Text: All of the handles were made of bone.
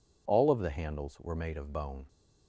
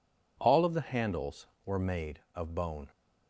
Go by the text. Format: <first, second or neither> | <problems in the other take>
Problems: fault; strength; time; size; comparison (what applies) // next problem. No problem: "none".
neither | none